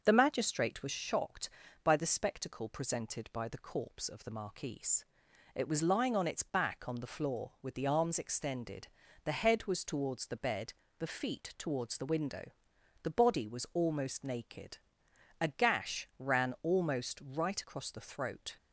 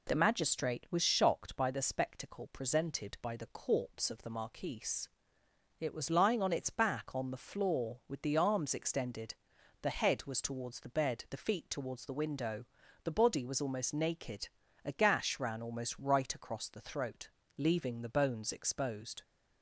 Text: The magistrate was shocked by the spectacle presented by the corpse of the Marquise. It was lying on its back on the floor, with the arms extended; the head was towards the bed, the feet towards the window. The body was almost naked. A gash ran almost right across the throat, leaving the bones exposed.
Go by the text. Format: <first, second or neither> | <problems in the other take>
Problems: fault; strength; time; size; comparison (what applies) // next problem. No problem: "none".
second | starts louder than the rest; until 1.0 s; 6.5 dB // stops before "leaving the bones exposed"; at 18.5 s